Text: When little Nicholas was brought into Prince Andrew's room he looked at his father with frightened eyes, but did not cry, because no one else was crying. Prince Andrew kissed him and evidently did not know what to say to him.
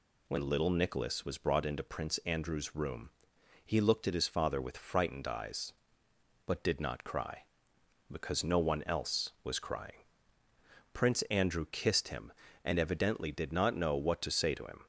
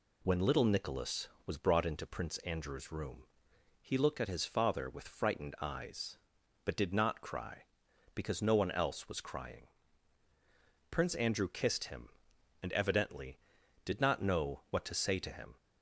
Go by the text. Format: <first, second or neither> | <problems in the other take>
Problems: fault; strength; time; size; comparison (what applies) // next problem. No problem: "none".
neither | pauses between "room" and "he"; noticeable; the same in both